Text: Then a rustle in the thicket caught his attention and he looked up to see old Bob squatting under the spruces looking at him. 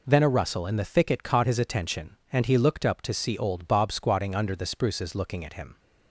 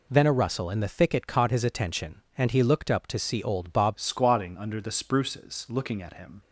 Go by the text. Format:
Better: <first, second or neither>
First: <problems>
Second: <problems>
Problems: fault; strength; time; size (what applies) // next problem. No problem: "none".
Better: first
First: none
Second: changes voice at "squatting"; from 3.9 s on; 2.5 s long